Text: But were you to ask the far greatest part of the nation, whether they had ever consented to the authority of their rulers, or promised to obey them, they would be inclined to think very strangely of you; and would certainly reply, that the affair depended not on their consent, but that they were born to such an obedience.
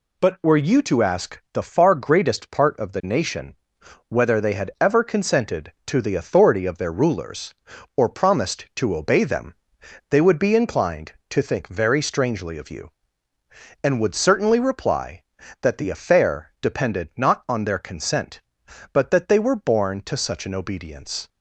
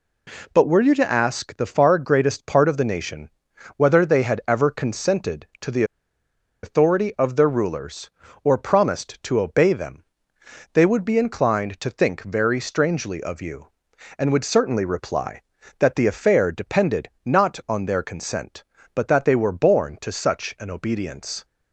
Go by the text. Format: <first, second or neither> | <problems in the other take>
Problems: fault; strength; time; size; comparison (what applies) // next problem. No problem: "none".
first | pauses between "the" and "authority"; noticeable; at 5.8 s; 0.79 s long